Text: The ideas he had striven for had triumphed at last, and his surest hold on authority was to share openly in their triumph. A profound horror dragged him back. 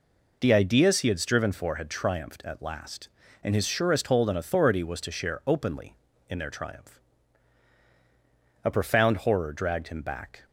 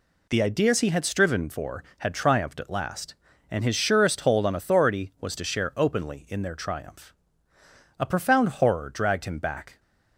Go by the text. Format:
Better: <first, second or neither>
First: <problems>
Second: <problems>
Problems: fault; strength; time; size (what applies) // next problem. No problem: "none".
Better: neither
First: none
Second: none